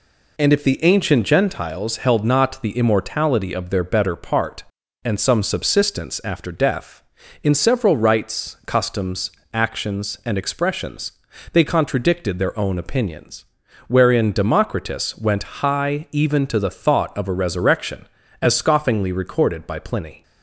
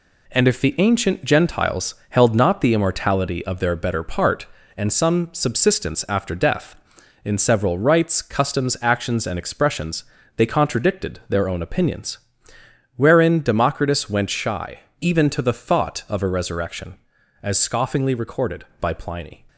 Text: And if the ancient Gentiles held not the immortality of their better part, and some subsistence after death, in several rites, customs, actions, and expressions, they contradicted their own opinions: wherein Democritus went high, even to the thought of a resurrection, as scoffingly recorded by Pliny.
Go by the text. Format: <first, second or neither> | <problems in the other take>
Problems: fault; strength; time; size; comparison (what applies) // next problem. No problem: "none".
first | pauses between "Gentiles" and "held"; slight; at 1.9 s; 0.16 s long // says "shy" for "high"; at 14.2 s